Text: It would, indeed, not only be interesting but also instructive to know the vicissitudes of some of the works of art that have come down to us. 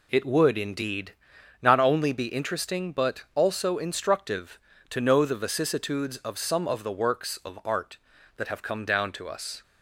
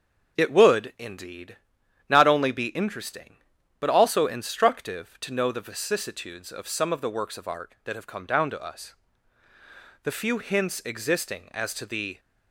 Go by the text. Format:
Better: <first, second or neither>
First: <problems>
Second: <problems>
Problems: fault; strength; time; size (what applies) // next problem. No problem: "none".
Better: first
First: none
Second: starts louder than the rest; until 1.4 s; 6.5 dB // goes on to say "The few hints existing as to the"; strong; from 10.0 s on; 2.1 s long